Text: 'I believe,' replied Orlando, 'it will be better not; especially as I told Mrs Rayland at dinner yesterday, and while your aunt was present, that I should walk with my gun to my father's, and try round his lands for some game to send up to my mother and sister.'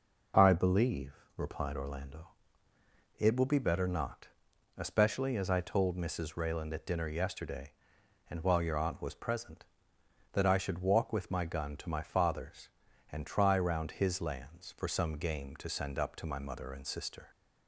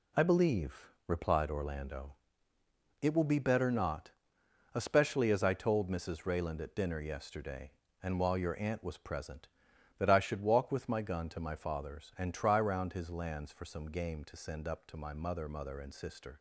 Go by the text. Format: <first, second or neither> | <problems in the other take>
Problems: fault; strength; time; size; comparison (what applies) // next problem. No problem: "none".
first | says "mother" twice; at 15.4 s